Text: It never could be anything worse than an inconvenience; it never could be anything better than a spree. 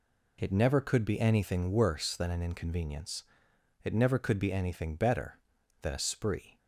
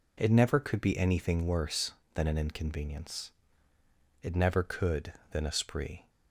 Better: first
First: none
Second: skips "be anything better"; at 5.2 s

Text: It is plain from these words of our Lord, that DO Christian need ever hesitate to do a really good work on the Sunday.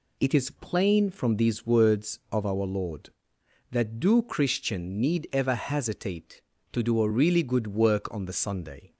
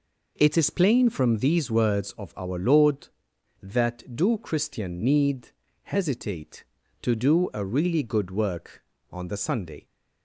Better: first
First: none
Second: skips "ever"; at 5.6 s

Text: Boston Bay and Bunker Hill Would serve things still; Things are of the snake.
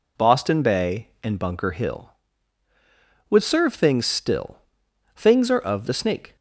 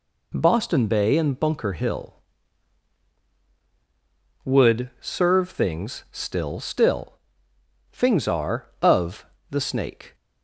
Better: first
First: none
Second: says "still" twice; at 6.5 s // pauses between "of" and "the"; slight; at 9.2 s; 0.24 s long

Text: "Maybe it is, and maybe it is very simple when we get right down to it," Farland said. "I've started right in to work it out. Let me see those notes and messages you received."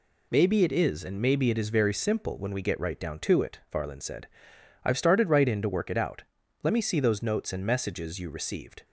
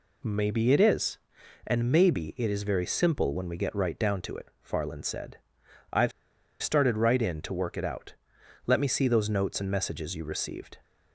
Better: first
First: none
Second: pauses between "I've" and "started"; noticeable; at 6.1 s; 0.51 s long

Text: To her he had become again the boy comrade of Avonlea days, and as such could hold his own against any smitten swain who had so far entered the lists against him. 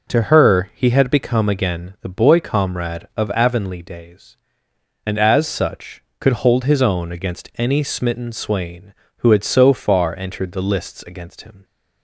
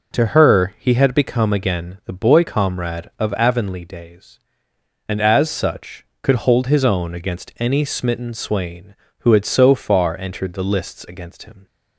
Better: neither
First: none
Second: none

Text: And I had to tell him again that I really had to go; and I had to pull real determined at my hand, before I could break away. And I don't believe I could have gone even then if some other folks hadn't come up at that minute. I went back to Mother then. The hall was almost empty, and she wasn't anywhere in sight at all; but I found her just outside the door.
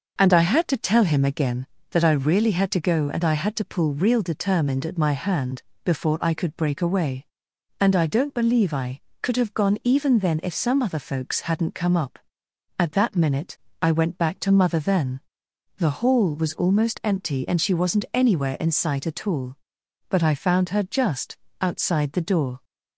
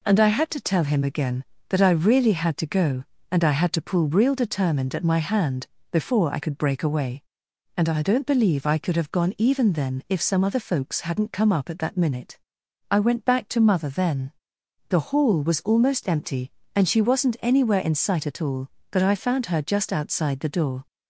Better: second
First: starts louder than the rest; noticeable; until 1.6 s; 6 dB // pauses between "just" and "outside"; slight; at 21.3 s; 0.22 s long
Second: none

